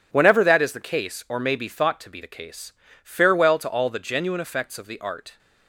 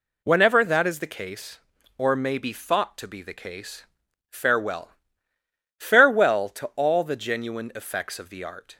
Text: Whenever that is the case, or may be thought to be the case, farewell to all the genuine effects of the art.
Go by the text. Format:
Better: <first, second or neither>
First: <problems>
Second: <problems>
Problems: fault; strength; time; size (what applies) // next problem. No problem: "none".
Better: first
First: none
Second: says "farewell" twice; at 5.7 s